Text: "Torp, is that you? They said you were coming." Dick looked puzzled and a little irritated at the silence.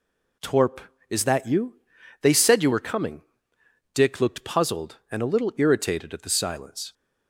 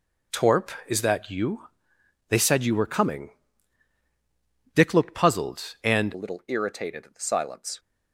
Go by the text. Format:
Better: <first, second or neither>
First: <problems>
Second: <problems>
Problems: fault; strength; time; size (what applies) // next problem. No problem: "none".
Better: first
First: none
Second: changes voice at "a"; from 6.1 s on; 1.6 s long